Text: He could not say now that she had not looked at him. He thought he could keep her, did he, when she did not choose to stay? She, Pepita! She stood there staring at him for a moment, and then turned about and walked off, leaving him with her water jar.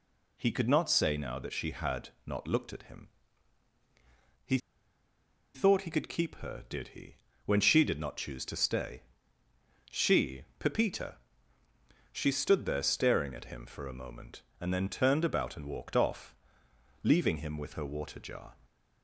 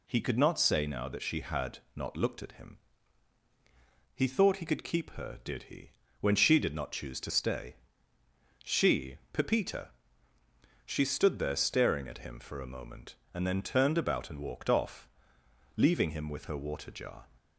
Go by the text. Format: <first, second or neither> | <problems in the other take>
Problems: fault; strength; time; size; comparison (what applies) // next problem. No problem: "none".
second | pauses between "had" and "not"; slight; at 2.0 s; 0.16 s long; slight in the second // pauses between "He" and "thought"; noticeable; at 4.5 s; 0.97 s long